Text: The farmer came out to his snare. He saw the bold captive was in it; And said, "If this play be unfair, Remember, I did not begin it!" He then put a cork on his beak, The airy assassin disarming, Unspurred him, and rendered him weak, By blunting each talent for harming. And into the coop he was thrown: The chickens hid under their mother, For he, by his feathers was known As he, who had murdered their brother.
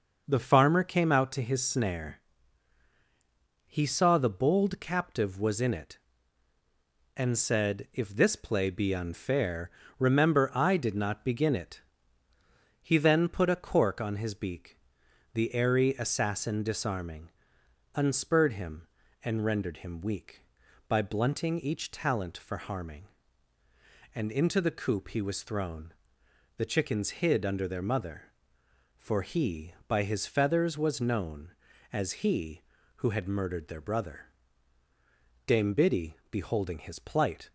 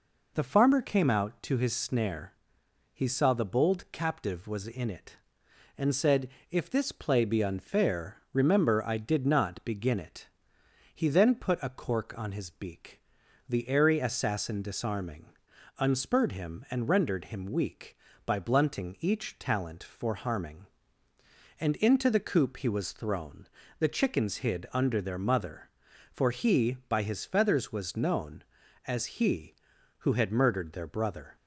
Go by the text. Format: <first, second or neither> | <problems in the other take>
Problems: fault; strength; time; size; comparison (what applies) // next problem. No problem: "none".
second | goes on to say "Dame Biddy beholding his plight"; strong; from 35.4 s on; 2.0 s long